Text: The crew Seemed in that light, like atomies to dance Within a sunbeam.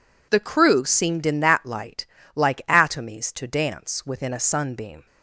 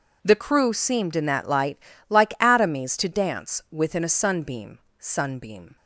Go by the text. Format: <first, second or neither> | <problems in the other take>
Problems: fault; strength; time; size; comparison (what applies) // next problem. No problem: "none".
first | says "sunbeam" twice; at 4.9 s